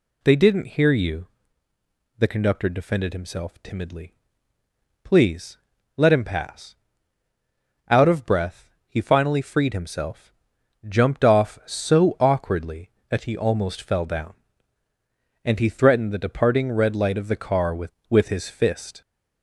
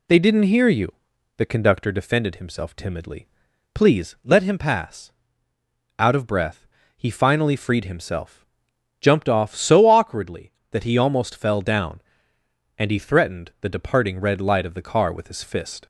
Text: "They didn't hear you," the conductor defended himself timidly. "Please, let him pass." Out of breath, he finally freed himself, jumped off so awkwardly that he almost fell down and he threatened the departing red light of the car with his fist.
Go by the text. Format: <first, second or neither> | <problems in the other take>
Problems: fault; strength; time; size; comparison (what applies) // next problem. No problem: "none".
second | says "with" twice; at 18.1 s